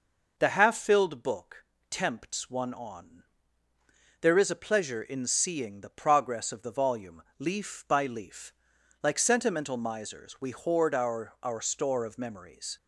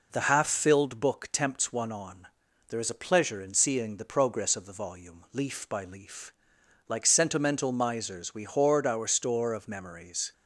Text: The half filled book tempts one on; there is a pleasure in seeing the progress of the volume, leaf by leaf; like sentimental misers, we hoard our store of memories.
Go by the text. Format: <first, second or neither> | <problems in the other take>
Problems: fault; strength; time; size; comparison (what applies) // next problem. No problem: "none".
second | pauses between "book" and "tempts"; slight; at 1.6 s; 0.24 s long // says "our" twice; at 11.4 s